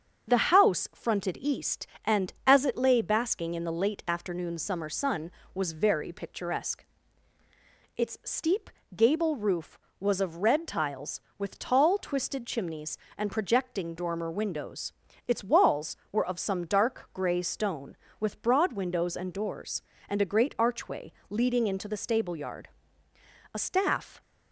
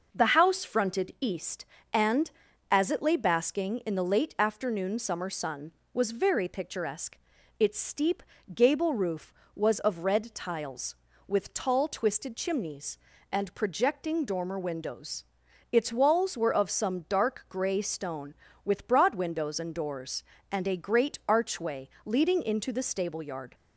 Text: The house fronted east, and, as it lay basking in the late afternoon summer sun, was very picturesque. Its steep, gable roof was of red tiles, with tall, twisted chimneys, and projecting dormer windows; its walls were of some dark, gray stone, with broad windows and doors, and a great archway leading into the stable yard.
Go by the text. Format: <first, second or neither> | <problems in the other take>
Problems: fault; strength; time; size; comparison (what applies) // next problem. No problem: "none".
second | starts louder than the rest; until 1.3 s; 6.5 dB // pauses between "archway" and "leading"; slight; at 21.1 s; 0.20 s long; slight in the second // goes on to say "A staff"; noticeable; from 23.5 s on; 0.66 s long